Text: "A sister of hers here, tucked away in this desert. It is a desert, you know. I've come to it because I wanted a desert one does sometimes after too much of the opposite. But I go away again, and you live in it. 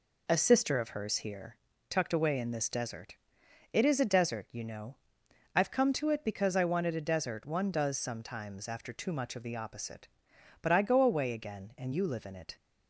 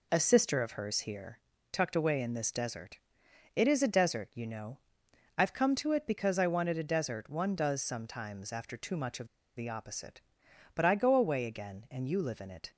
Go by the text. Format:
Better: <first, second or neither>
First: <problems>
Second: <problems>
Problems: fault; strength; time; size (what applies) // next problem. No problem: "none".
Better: first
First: none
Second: pauses between "of" and "the"; slight; at 9.2 s; 0.29 s long